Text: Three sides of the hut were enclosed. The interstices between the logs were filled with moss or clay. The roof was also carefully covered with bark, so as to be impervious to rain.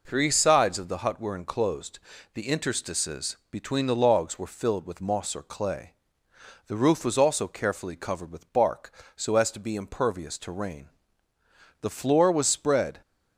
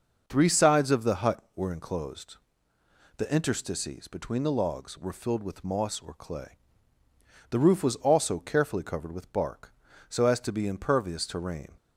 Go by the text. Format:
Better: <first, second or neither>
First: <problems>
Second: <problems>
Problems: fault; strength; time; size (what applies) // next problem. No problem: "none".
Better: second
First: goes on to say "The floor was spread"; noticeable; from 11.8 s on; 1.2 s long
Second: none